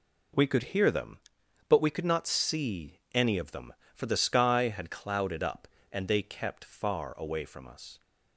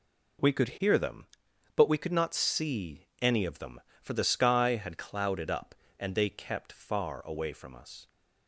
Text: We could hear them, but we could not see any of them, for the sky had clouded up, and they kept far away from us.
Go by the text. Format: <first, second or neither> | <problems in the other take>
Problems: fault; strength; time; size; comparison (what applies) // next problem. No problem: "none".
neither | none